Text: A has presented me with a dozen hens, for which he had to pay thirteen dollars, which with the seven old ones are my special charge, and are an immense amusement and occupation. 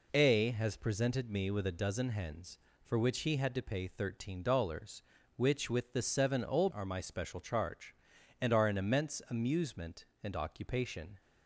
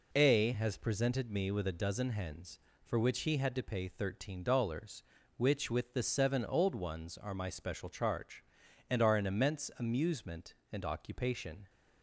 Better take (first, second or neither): second